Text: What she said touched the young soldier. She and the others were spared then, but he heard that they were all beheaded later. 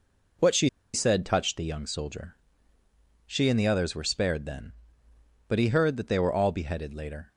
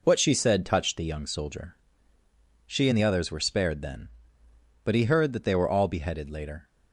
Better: second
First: pauses between "she" and "said"; slight; at 0.6 s; 0.24 s long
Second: none

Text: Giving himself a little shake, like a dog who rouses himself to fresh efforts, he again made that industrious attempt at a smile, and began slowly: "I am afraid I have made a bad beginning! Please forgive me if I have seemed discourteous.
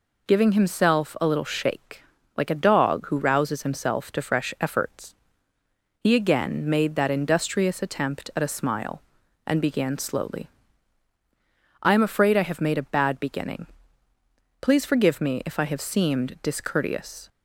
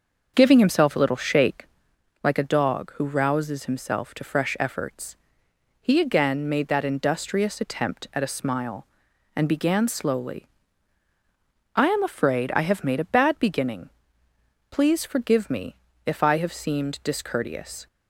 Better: first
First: none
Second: starts louder than the rest; until 2.0 s; 6.5 dB // pauses between "me" and "if"; slight; at 15.7 s; 0.28 s long

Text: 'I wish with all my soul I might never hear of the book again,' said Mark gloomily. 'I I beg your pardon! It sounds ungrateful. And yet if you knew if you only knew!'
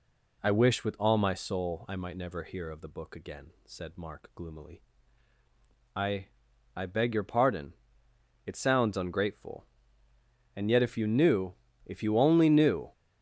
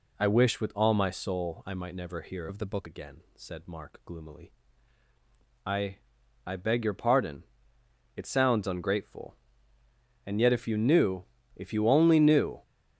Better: first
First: pauses between "I" and "I"; noticeable; at 6.2 s; 0.50 s long // pauses between "knew" and "if"; slight; at 11.5 s; 0.32 s long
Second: changes voice from "of" to "book"; from 2.4 to 2.8 s; 0.4 s long // pauses between "I" and "I"; noticeable; at 5.9 s; 0.50 s long // pauses between "knew" and "if"; slight; at 11.2 s; 0.32 s long

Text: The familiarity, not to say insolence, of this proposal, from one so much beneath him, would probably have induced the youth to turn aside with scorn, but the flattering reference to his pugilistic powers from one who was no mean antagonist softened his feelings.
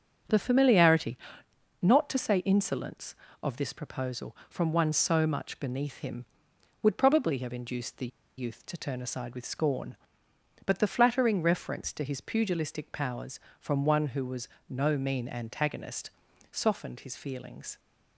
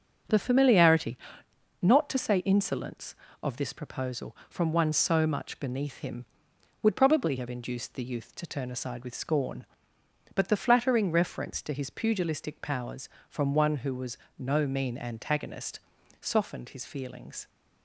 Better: second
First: starts louder than the rest; strong; until 1.9 s; 7 dB // pauses between "the" and "youth"; slight; at 8.0 s; 0.30 s long // pauses between "was" and "no"; slight; at 14.4 s; 0.22 s long // pauses between "antagonist" and "softened"; at 16.1 s; 0.40 s long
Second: starts louder than the rest; strong; until 1.9 s; 7 dB // pauses between "was" and "no"; slight; at 14.1 s; 0.22 s long // pauses between "antagonist" and "softened"; at 15.8 s; 0.40 s long

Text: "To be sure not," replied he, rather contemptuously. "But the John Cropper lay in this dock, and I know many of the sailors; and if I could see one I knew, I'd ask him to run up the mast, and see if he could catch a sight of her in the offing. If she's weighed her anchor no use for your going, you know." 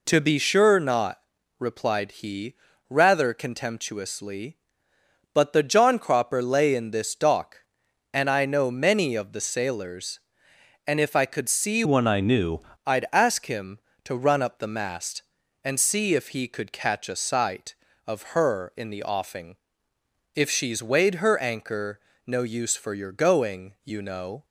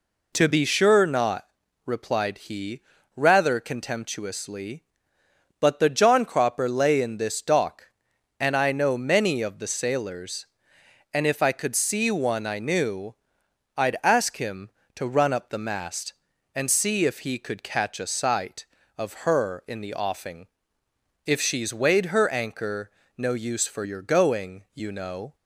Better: second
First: changes voice from "one" to "knew"; from 11.8 to 12.5 s; 0.7 s long // pauses between "anchor" and "no"; slight; at 21.9 s; 0.28 s long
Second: pauses between "anchor" and "no"; slight; at 22.8 s; 0.28 s long

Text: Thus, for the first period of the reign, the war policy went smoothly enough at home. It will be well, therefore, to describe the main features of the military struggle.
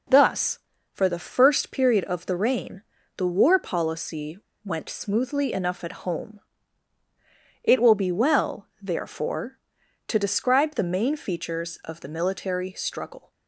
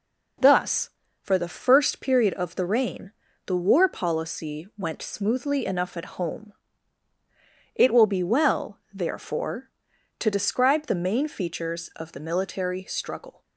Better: second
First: pauses between "policy" and "went"; slight; at 4.3 s; 0.26 s long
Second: none

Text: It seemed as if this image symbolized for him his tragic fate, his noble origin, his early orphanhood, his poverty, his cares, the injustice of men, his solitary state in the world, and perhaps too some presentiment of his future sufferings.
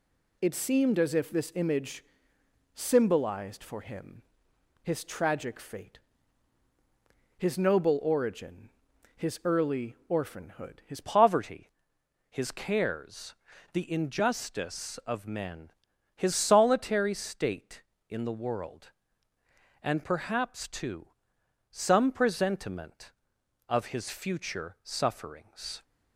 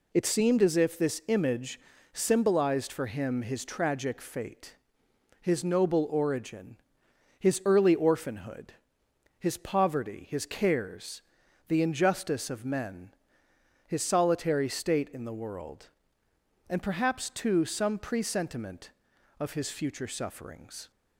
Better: second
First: pauses between "image" and "symbolized"; noticeable; at 2.0 s; 0.70 s long // pauses between "him" and "his"; noticeable; at 4.2 s; 0.60 s long // changes voice at "poverty"; from 11.0 s on; 14.8 s long // pauses between "too" and "some"; noticeable; at 21.0 s; 0.64 s long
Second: pauses between "image" and "symbolized"; slight; at 1.8 s; 0.32 s long

